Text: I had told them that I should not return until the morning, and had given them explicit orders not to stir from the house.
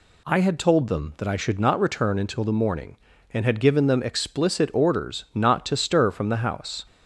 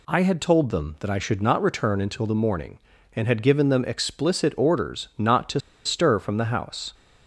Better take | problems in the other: first | pauses between "to" and "stir"; slight; at 5.5 s; 0.26 s long

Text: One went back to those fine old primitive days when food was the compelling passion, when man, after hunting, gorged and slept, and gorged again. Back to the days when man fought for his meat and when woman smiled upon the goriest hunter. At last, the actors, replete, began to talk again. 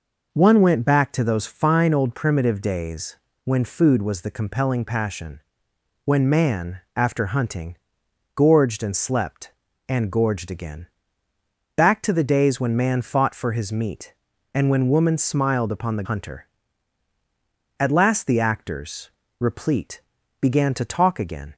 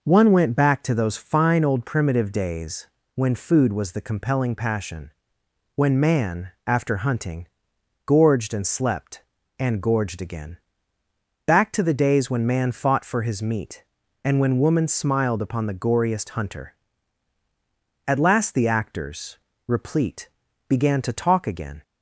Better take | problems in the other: second | pauses between "days" and "when"; slight; at 3.1 s; 0.28 s long; slight in the second // skips "goriest"; at 16.0 s

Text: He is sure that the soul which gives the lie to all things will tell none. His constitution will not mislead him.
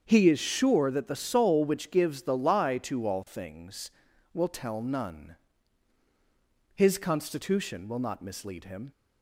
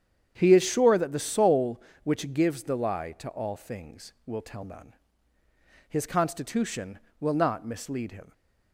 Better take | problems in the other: neither | starts louder than the rest; the same in both

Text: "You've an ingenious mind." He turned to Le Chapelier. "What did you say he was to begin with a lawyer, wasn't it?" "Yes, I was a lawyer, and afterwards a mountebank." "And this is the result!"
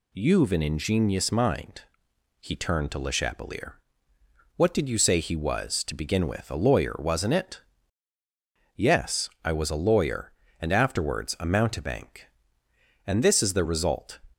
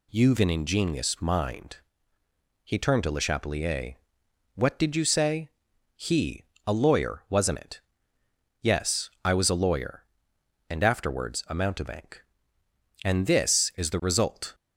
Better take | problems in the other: first | pauses between "say" and "he"; noticeable; at 5.5 s; 0.46 s long // skips "was to begin with"; at 6.5 s

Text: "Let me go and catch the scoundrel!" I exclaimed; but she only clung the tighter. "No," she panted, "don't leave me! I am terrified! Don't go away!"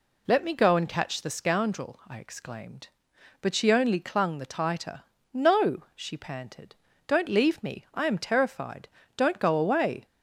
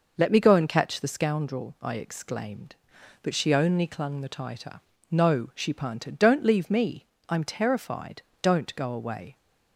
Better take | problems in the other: neither | none

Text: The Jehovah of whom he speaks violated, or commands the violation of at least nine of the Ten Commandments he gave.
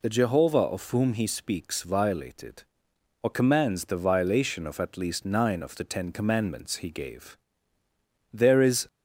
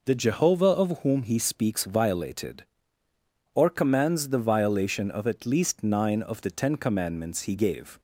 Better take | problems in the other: second | goes on to say "There is"; from 8.3 s on; 0.54 s long

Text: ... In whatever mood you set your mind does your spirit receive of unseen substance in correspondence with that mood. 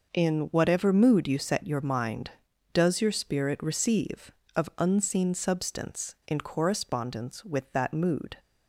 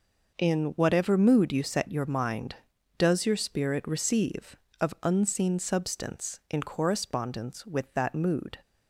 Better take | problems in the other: neither | none

